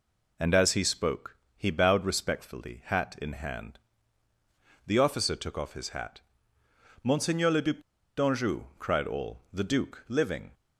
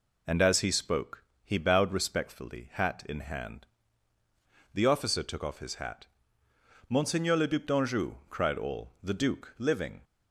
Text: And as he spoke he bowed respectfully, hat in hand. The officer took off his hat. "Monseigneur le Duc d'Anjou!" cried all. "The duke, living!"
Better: second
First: pauses between "spoke" and "he"; slight; at 1.3 s; 0.20 s long // pauses between "Duc" and "d'Anjou"; at 7.7 s; 0.37 s long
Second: pauses between "spoke" and "he"; slight; at 1.2 s; 0.20 s long

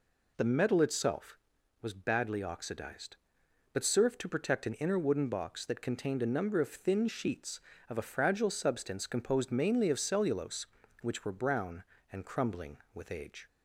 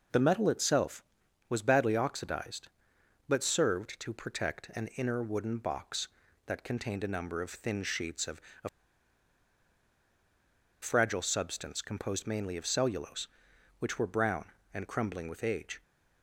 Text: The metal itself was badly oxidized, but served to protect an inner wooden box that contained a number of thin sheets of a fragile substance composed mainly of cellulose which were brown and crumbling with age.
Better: first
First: none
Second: pauses between "of" and "a"; slight; at 8.4 s; 0.20 s long // pauses between "a" and "fragile"; strong; at 8.6 s; 2.1 s long

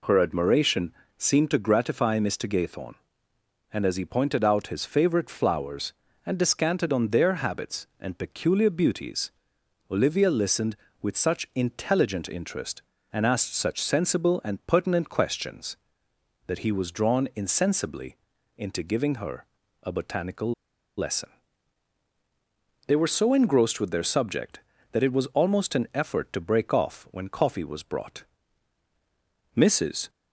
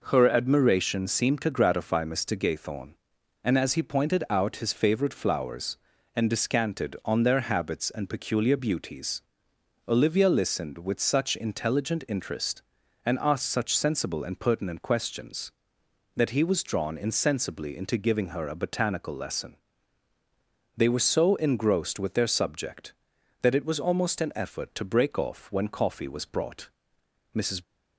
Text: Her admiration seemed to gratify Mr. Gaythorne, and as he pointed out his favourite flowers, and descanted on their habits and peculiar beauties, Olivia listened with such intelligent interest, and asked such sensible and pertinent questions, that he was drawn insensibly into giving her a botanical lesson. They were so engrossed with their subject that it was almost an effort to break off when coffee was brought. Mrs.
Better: second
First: pauses between "admiration" and "seemed"; slight; at 0.9 s; 0.24 s long // pauses between "insensibly" and "into"; at 18.1 s; 0.42 s long // pauses between "her" and "a"; at 19.4 s; 0.38 s long // pauses between "botanical" and "lesson"; at 20.5 s; 0.45 s long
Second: none

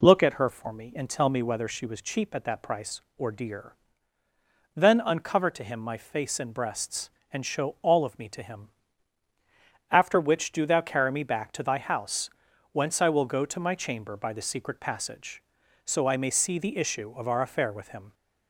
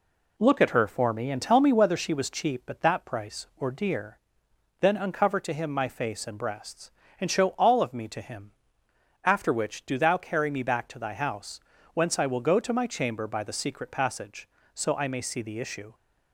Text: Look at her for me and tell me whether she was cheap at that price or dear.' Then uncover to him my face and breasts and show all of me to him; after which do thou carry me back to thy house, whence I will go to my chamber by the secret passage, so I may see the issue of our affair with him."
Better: first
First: none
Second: stops before "of our affair with him"; at 15.9 s

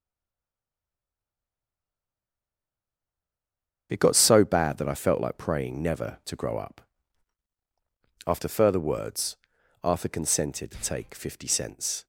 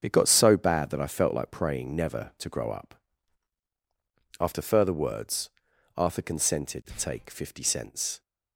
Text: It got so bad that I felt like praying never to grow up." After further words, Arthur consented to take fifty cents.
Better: second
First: stays silent before the first word; strong; until 3.8 s; 3.8 s long // starts louder than the rest; strong; until 4.9 s; 7 dB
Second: starts louder than the rest; strong; until 1.0 s; 7 dB

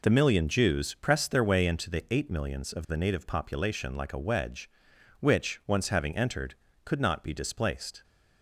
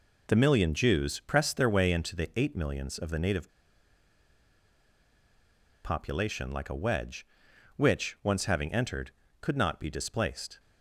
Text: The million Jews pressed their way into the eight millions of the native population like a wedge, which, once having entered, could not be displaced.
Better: first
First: none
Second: pauses between "native" and "population"; strong; at 3.4 s; 2.3 s long

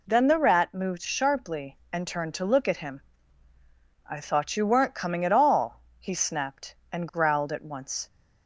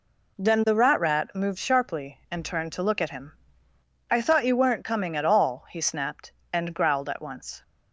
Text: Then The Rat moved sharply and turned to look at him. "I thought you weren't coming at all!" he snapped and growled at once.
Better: first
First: none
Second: says "Rat" twice; at 1.0 s

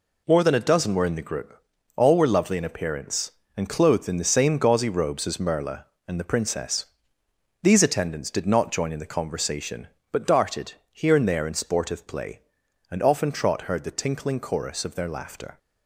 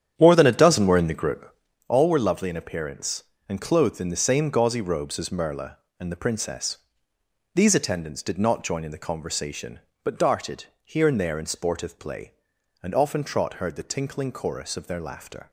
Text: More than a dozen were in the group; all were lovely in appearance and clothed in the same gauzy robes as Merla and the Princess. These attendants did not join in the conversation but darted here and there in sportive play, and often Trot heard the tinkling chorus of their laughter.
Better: first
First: pauses between "darted" and "here"; slight; at 10.7 s; 0.18 s long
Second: starts louder than the rest; strong; until 1.9 s; 9.5 dB // pauses between "darted" and "here"; slight; at 10.6 s; 0.18 s long

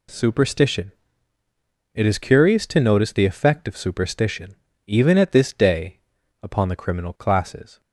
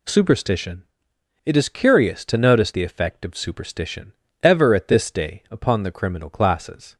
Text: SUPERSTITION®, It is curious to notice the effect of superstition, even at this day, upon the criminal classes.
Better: first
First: none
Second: says "ever" for "even"; at 4.4 s

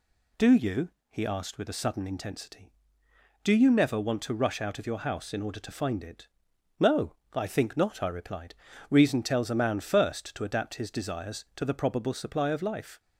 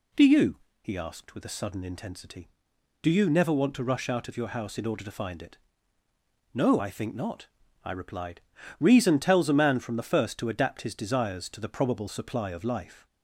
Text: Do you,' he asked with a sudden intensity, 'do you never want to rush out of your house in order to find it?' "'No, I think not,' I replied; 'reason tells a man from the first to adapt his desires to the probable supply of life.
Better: second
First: skips "from the"; at 9.7 s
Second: none

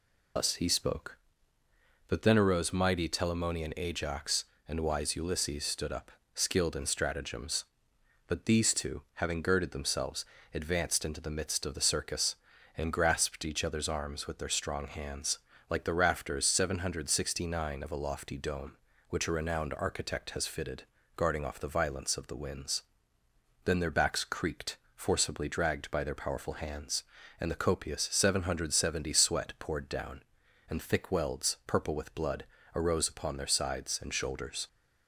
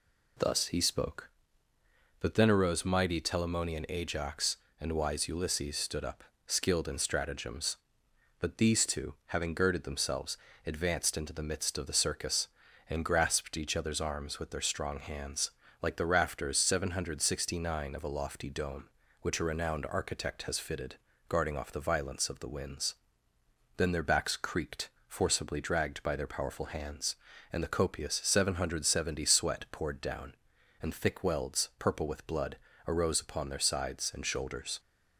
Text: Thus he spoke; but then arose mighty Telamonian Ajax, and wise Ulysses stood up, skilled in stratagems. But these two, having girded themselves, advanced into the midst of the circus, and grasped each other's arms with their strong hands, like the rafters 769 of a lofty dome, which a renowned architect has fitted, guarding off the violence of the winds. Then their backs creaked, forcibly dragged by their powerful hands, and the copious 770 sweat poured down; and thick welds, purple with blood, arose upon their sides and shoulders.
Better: second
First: loses the start of "Thus"; at 0.3 s; 115 ms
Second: none

